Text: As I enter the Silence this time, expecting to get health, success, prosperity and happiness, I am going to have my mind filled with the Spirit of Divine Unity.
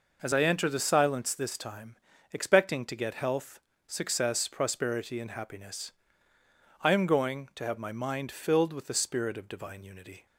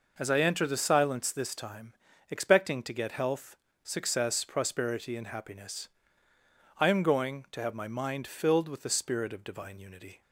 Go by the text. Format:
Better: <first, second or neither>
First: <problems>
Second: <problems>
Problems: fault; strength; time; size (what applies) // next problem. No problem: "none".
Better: neither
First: none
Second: none